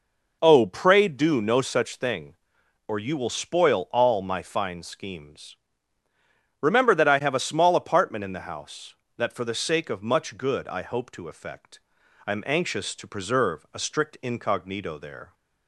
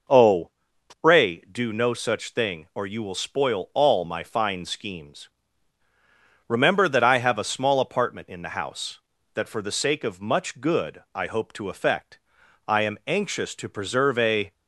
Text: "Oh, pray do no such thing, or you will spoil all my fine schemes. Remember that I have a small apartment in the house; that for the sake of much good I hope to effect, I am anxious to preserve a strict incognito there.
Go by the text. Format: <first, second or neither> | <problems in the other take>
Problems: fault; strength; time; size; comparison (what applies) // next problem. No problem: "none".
first | stops before "strict incognito there"; at 14.5 s